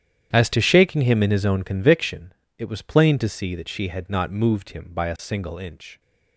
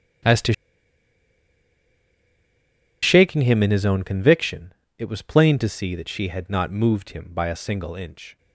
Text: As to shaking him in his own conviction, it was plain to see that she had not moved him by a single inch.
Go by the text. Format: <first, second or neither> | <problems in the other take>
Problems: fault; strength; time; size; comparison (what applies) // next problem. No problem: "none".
first | starts louder than the rest; strong; until 3.7 s; 10 dB; strong in the first // pauses between "to" and "shaking"; strong; at 0.5 s; 2.4 s long